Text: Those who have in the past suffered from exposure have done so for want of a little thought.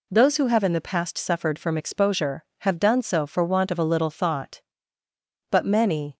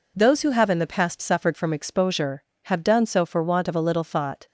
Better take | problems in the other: second | goes on to say "But many"; noticeable; from 5.5 s on; 0.66 s long

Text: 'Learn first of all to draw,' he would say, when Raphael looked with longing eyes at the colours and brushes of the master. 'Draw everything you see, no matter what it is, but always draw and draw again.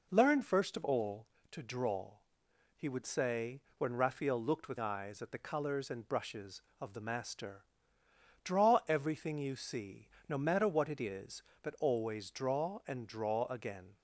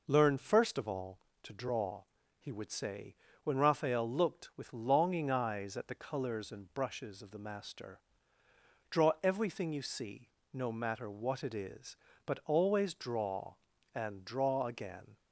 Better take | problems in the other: second | skips "longing"; at 4.7 s

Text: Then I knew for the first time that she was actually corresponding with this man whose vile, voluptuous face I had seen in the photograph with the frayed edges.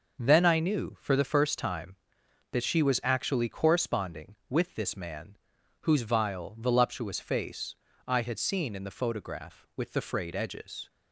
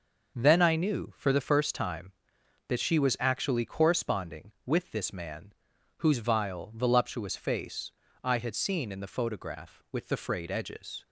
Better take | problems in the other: neither | starts louder than the rest; noticeable; the same in both // pauses between "man" and "whose"; noticeable; the same in both // pauses between "face" and "I"; slight; the same in both

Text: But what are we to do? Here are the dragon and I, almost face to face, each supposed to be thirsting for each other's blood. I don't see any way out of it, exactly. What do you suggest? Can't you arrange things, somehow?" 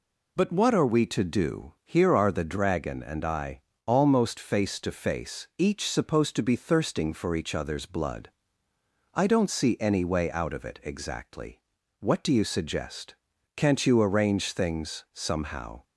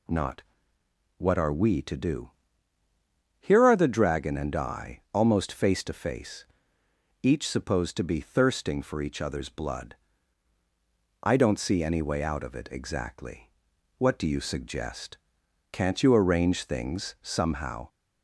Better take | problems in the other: first | says "Not" for "But"; at 0.0 s

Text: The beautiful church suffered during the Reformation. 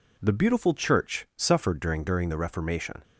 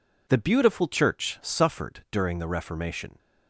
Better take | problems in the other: second | says "during" twice; at 2.0 s

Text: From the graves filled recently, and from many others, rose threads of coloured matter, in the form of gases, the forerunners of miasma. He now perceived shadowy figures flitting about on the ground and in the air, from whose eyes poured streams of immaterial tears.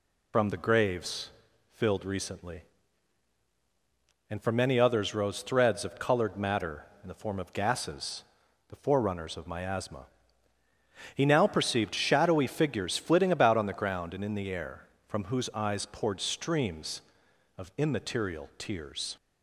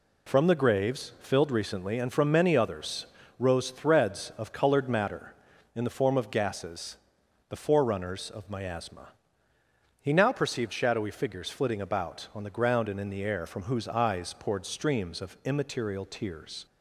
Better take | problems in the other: second | loses the start of "From"; at 0.3 s; 70 ms // pauses between "graves" and "filled"; at 1.2 s; 0.42 s long

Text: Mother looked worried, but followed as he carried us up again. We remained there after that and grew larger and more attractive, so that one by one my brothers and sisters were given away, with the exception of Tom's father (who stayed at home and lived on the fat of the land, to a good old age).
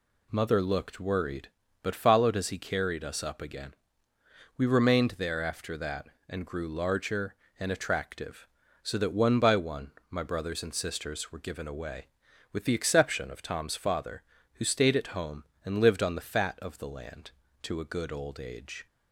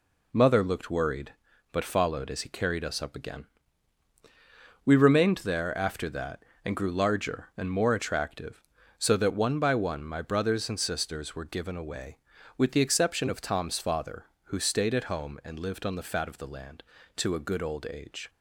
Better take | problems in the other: second | skips "more"; at 7.7 s // pauses between "one" and "my"; slight; at 9.9 s; 0.18 s long

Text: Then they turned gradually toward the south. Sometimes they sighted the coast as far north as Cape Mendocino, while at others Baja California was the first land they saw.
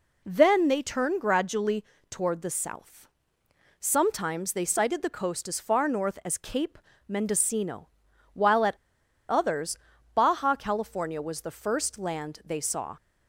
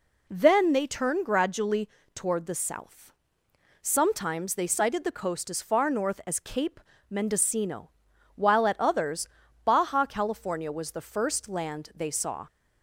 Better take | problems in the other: second | pauses between "gradually" and "toward"; slight; at 1.8 s; 0.26 s long; slight in the second // pauses between "Cape" and "Mendocino"; slight; at 6.7 s; 0.32 s long; slight in the second // pauses between "at" and "others"; noticeable; at 8.7 s; 0.54 s long // pauses between "others" and "Baja"; at 9.7 s; 0.38 s long; also in the second

